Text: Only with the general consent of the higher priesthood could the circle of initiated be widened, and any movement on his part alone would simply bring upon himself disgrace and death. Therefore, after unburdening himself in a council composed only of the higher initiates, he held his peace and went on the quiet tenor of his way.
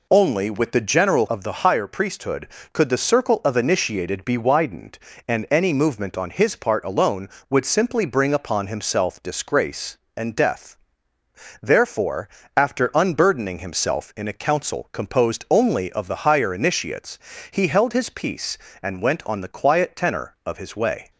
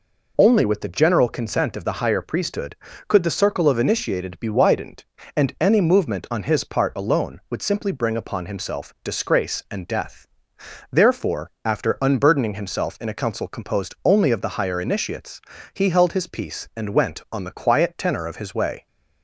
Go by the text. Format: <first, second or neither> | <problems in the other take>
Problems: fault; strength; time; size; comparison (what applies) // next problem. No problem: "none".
second | skips "consent"; at 1.2 s